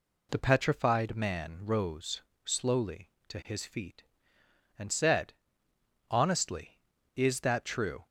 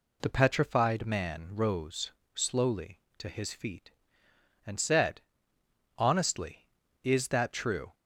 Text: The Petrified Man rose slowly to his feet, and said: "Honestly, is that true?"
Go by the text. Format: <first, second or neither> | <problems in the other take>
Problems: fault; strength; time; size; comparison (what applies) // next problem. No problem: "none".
neither | pauses between "rose" and "slowly"; slight; the same in both